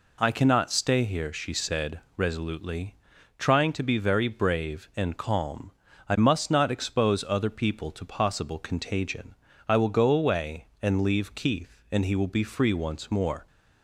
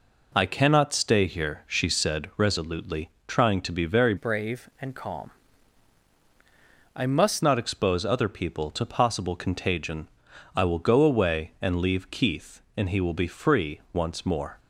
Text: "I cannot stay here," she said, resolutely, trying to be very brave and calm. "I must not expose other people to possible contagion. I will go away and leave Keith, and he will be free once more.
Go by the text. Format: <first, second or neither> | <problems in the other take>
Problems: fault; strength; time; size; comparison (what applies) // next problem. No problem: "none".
first | changes voice from "brave" to "must"; from 4.1 to 7.4 s; 3.3 s long